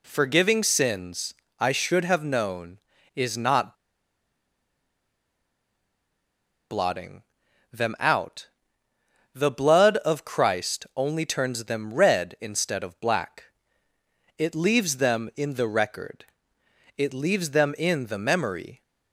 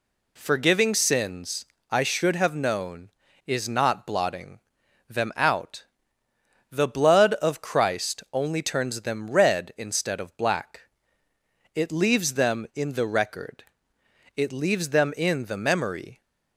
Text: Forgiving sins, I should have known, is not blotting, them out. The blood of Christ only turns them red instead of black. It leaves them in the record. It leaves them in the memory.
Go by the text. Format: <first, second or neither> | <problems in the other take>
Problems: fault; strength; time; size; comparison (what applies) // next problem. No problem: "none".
second | pauses between "not" and "blotting"; strong; at 3.7 s; 2.9 s long